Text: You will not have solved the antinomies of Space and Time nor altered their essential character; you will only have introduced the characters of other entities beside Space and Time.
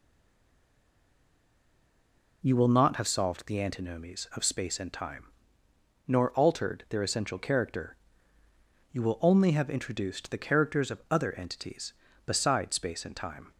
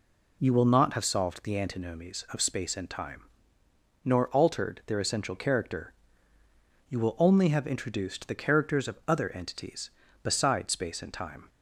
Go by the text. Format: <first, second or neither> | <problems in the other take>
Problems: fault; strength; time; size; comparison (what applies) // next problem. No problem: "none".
second | stays silent before the first word; until 2.4 s; 2.4 s long // pauses between "Time" and "nor"; noticeable; at 5.2 s; 0.82 s long; noticeable in the second